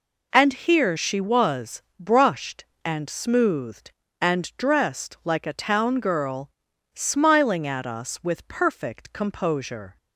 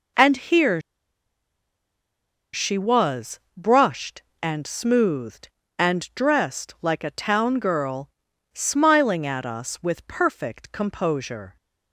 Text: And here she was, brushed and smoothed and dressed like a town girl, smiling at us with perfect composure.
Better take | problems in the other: first | pauses between "here" and "she"; strong; at 0.8 s; 1.7 s long

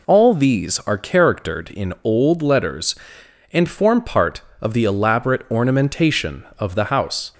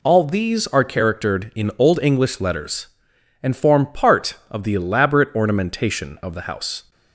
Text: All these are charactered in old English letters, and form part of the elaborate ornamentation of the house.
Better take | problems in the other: second | skips "English"; at 2.4 s

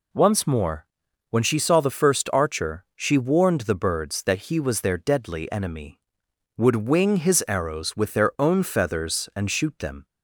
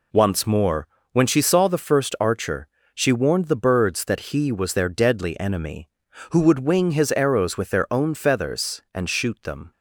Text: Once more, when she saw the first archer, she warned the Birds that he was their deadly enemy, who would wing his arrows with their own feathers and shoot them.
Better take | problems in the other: second | skips "who"; at 6.2 s

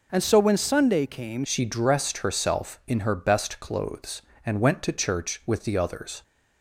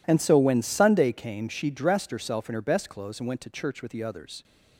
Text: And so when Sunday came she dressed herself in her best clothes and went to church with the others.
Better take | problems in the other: second | changes voice at "she"; from 1.4 s on; 4.8 s long

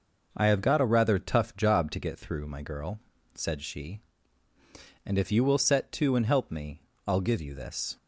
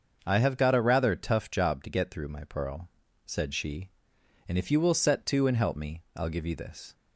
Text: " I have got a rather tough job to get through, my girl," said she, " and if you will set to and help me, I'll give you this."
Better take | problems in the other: first | starts louder than the rest; until 1.2 s; 7 dB // says "pearl" for "girl"; at 2.4 s

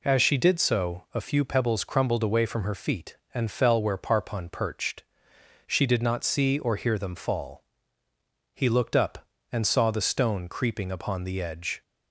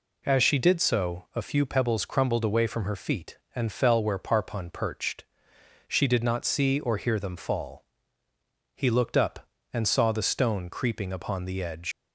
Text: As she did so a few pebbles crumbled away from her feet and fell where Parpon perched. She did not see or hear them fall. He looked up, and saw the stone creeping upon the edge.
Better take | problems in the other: first | leaves "edge" unfinished; at 11.9 s; 110 ms

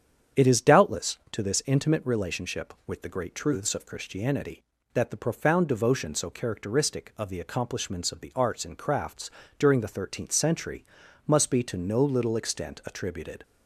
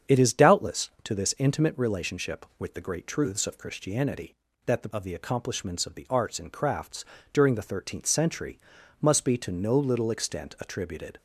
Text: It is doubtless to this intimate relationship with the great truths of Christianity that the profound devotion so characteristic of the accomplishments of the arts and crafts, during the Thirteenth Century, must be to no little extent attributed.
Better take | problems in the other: first | starts louder than the rest; strong; until 1.2 s; 8 dB; strong in the first // skips "profound devotion so characteristic"; at 4.9 s

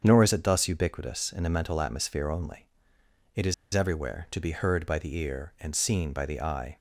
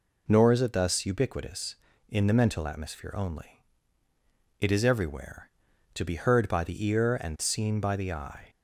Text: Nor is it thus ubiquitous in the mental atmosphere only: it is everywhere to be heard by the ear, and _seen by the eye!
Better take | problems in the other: second | starts louder than the rest; strong; until 1.0 s; 7.5 dB // pauses between "is" and "everywhere"; slight; at 3.5 s; 0.20 s long

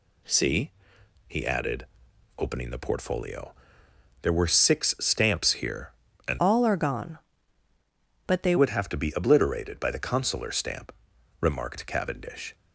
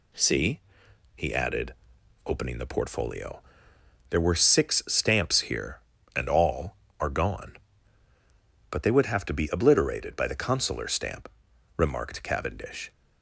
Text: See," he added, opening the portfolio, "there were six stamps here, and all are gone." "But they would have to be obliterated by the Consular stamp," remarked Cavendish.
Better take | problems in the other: second | changes voice from "all" to "they"; from 6.3 to 8.5 s; 2.2 s long

